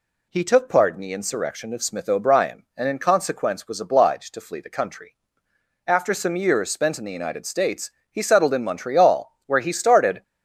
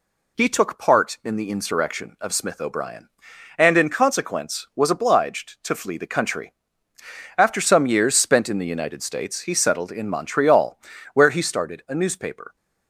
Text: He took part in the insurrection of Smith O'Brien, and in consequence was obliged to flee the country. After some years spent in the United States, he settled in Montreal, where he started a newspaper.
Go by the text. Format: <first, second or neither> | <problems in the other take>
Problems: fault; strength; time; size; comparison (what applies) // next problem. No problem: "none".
second | stops before "a newspaper"; at 10.2 s